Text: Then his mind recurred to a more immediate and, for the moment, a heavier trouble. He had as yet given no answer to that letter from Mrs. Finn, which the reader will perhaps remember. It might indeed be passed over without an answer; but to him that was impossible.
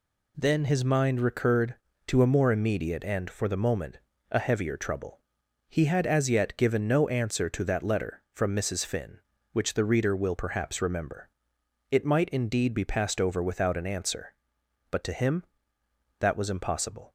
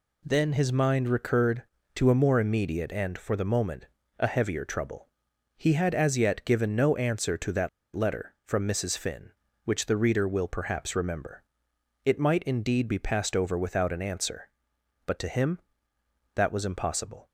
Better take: first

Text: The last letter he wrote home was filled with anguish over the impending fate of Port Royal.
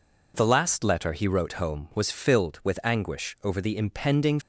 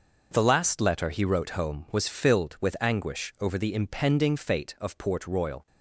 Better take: second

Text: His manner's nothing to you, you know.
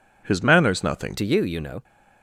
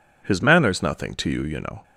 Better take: second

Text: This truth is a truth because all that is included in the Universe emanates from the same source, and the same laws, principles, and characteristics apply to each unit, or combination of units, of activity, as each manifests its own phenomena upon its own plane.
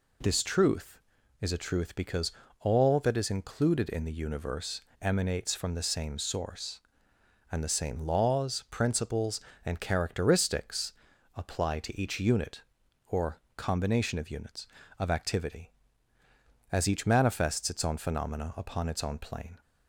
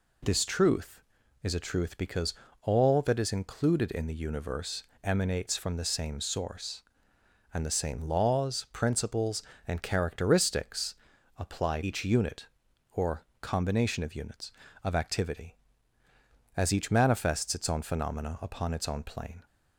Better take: first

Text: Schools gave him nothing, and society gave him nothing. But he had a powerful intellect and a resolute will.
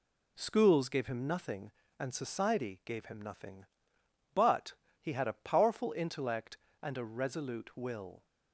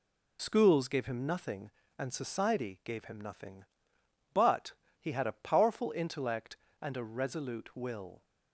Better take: first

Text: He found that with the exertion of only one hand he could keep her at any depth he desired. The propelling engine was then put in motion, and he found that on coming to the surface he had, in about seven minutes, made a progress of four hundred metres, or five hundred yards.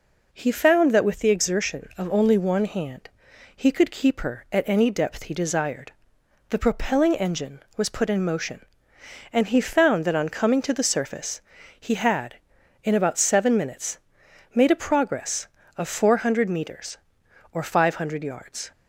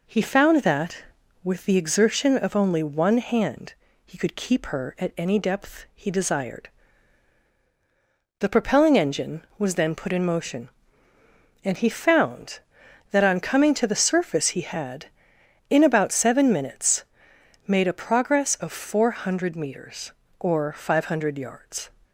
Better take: second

